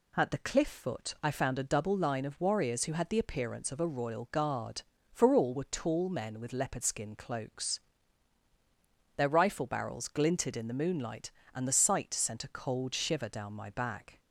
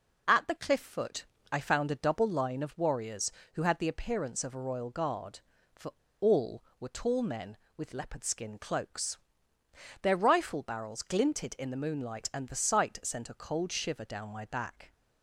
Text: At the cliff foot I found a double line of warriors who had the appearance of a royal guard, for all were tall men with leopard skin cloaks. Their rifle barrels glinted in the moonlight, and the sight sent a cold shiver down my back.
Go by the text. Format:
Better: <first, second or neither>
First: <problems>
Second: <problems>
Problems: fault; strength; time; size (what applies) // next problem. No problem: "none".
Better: first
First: none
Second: pauses between "foot" and "I"; slight; at 1.2 s; 0.24 s long // pauses between "for" and "all"; slight; at 5.9 s; 0.29 s long